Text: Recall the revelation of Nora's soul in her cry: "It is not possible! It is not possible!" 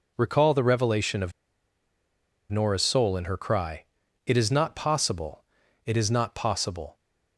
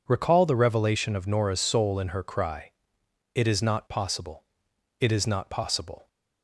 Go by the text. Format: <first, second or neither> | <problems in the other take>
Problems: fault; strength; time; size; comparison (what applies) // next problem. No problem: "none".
second | pauses between "of" and "Nora's"; at 1.3 s; 1.1 s long